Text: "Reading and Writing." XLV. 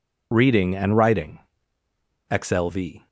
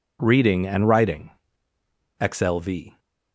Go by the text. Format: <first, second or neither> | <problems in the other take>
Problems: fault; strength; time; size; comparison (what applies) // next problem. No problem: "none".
second | loses the start of "Reading"; at 0.3 s; 35 ms